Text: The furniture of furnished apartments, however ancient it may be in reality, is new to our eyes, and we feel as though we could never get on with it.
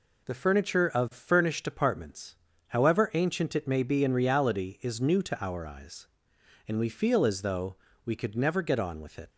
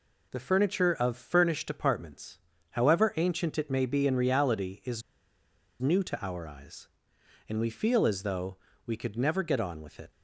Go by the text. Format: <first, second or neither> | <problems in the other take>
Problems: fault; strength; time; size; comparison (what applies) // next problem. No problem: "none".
first | pauses between "is" and "new"; noticeable; at 5.0 s; 0.79 s long // pauses between "though" and "we"; slight; at 8.5 s; 0.28 s long; slight in the first